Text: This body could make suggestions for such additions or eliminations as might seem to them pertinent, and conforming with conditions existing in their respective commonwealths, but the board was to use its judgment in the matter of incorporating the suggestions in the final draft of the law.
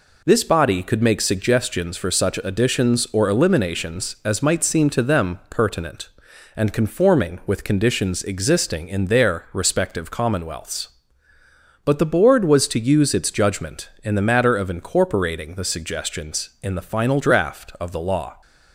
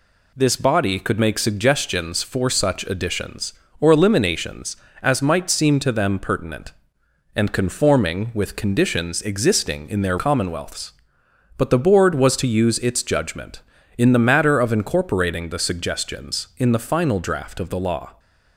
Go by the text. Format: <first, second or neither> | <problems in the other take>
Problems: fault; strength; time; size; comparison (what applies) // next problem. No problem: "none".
first | skips "respective"; at 10.1 s